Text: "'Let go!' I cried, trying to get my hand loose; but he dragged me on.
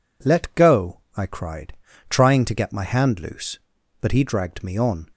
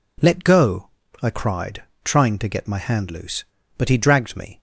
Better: first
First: none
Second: stops before "on"; at 4.5 s

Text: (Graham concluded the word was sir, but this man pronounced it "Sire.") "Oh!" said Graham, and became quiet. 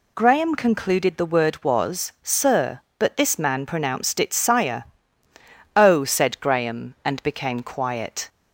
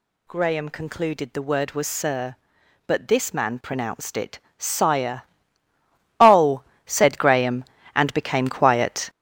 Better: first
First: none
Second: gets louder; strong; throughout; 7.5 dB // pauses between "it" and "Sire"; slight; at 4.3 s; 0.22 s long

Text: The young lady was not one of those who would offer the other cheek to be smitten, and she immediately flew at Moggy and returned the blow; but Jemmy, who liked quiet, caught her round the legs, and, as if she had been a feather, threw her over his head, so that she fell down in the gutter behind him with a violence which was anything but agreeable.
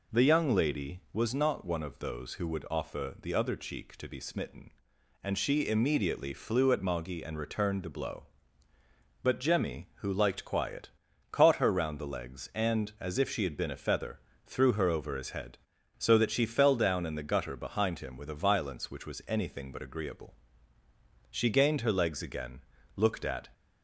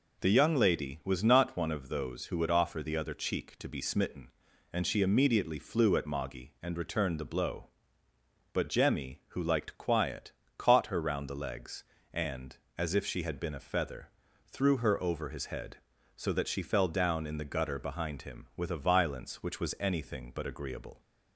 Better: second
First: goes on to say "She gained her legs again looked at"; strong; from 21.3 s on; 2.1 s long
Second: none

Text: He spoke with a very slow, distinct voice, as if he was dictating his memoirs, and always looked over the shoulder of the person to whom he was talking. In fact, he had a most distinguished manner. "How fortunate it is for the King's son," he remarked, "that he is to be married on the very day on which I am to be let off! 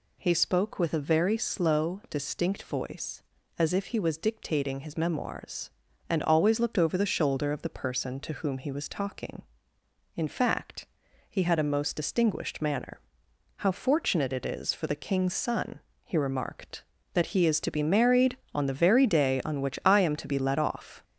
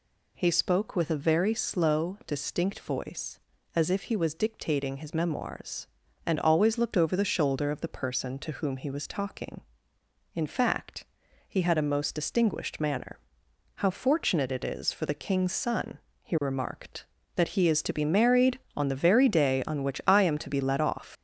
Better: first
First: none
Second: leaves "off" unfinished; at 21.1 s; 100 ms

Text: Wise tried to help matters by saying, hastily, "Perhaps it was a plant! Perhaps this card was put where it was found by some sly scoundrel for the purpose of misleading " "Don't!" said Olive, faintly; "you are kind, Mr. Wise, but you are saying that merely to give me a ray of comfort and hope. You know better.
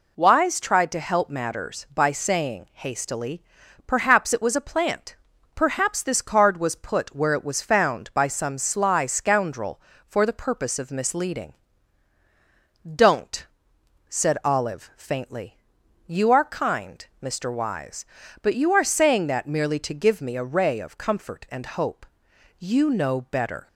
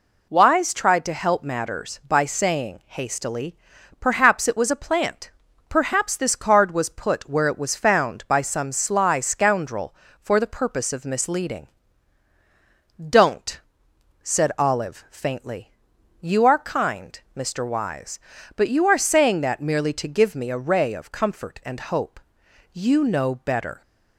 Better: neither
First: none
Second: none

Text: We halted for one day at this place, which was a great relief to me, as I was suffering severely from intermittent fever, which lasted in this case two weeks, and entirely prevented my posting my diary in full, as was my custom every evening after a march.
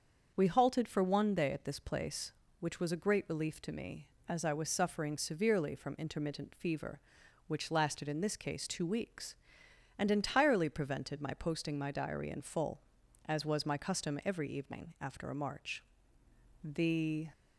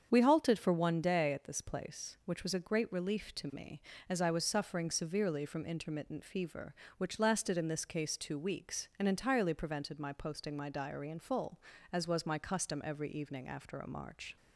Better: second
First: starts louder than the rest; until 1.3 s; 6.5 dB // goes on to say "The"; noticeable; from 16.6 s on; 0.66 s long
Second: starts louder than the rest; strong; until 1.1 s; 7.5 dB

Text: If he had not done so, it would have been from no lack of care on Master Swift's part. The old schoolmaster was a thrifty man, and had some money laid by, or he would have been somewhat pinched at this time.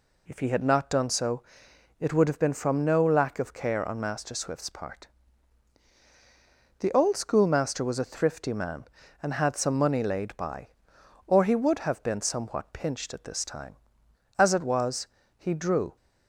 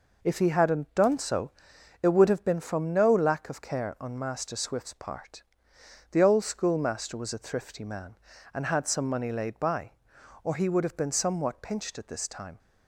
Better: second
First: goes on to say "As it was he drew"; from 14.3 s on; 1.5 s long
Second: none

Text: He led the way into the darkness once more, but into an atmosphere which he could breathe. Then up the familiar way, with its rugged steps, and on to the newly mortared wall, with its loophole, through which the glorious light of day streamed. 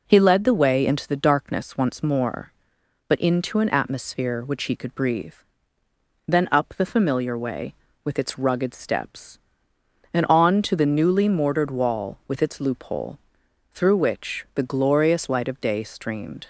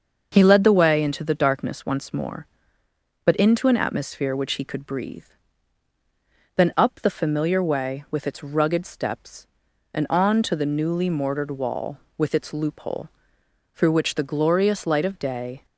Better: first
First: none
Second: starts louder than the rest; until 1.3 s; 6.5 dB // stops before "streamed"; at 15.6 s

